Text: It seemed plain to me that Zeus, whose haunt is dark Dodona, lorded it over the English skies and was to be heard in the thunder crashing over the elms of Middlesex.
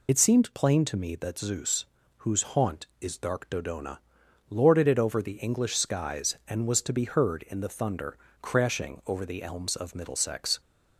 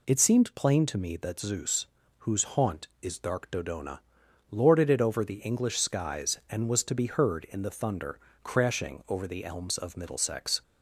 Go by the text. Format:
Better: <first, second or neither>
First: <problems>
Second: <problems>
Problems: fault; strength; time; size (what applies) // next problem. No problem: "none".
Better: second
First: loses the start of "It"; at 0.0 s; 35 ms // pauses between "thunder" and "crashing"; slight; at 8.1 s; 0.24 s long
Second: pauses between "thunder" and "crashing"; slight; at 8.1 s; 0.24 s long